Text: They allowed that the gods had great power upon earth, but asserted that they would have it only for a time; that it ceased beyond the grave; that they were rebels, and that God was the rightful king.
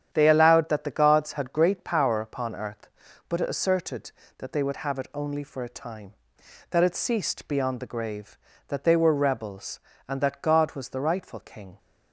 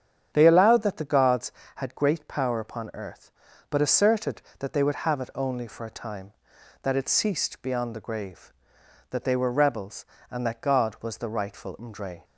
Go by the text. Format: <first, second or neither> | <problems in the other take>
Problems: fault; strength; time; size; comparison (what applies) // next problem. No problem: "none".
first | starts louder than the rest; strong; until 1.3 s; 8.5 dB; strong in the first // says "mdre" for "king"; at 11.7 s